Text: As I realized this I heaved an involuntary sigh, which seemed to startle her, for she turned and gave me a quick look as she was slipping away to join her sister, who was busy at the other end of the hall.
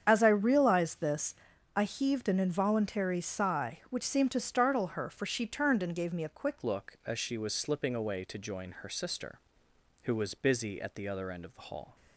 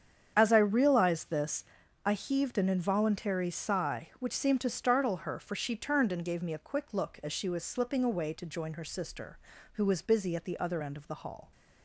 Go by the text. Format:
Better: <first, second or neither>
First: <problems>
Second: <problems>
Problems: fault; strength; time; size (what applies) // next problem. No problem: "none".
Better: second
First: starts louder than the rest; strong; until 1.0 s; 8 dB // pauses between "this" and "I"; at 1.3 s; 0.42 s long // changes voice at "look"; from 6.6 s on; 5.3 s long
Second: starts louder than the rest; strong; until 1.3 s; 8 dB // pauses between "this" and "I"; at 1.6 s; 0.42 s long